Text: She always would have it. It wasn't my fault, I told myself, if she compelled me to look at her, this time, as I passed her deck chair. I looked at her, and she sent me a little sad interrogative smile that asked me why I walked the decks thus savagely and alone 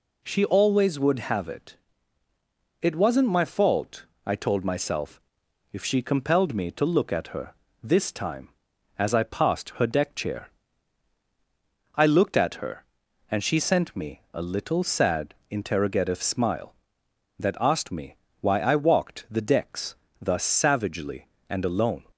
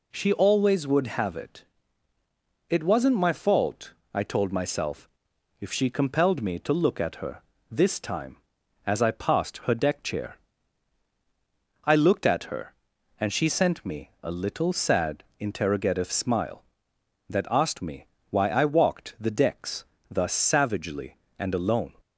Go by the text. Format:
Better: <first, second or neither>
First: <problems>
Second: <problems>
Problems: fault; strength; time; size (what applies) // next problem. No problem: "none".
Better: neither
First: pauses between "sad" and "interrogative"; slight; at 15.3 s; 0.16 s long // pauses between "me" and "why"; slight; at 18.1 s; 0.24 s long // pauses between "decks" and "thus"; slight; at 19.9 s; 0.26 s long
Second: pauses between "sad" and "interrogative"; slight; at 15.2 s; 0.16 s long // pauses between "me" and "why"; slight; at 18.0 s; 0.23 s long // pauses between "decks" and "thus"; slight; at 19.8 s; 0.26 s long